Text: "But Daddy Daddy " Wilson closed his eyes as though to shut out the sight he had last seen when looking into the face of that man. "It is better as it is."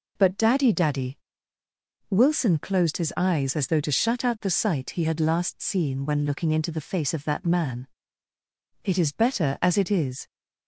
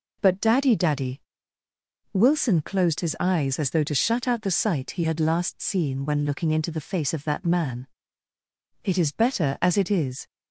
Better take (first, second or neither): neither